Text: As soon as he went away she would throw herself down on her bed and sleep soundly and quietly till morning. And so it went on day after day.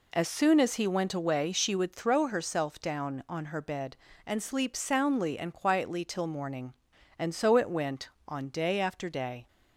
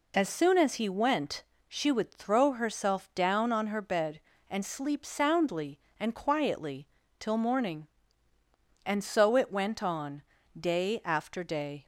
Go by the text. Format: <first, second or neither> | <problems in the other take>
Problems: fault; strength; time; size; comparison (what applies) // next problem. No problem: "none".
first | skips "away"; at 1.5 s // pauses between "quietly" and "till"; slight; at 6.8 s; 0.32 s long // pauses between "on" and "day"; slight; at 10.2 s; 0.34 s long